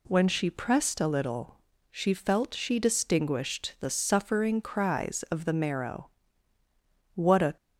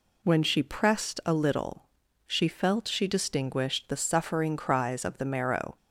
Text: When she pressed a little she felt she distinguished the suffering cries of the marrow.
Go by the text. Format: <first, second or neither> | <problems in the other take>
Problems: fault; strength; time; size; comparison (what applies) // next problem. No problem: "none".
second | pauses between "little" and "she"; slight; at 1.5 s; 0.34 s long; also in the second // goes on to say "What a"; slight; from 7.1 s on; 0.42 s long